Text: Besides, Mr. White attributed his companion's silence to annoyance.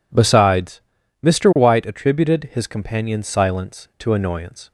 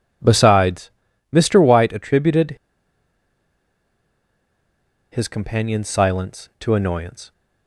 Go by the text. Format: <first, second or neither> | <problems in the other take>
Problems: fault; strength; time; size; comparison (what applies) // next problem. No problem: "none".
first | pauses between "attributed" and "his"; strong; at 2.5 s; 2.5 s long